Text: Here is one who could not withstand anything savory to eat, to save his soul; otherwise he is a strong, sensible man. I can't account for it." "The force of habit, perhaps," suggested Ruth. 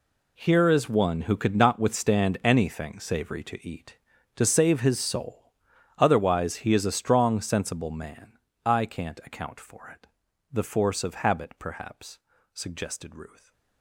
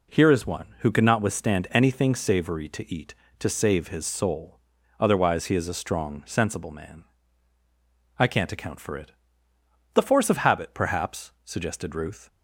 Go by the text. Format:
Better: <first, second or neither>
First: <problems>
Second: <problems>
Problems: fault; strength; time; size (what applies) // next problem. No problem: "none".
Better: second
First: gets quieter; strong; throughout; 15 dB // stays silent after the last word; slight; from 13.2 s on; 0.6 s long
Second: none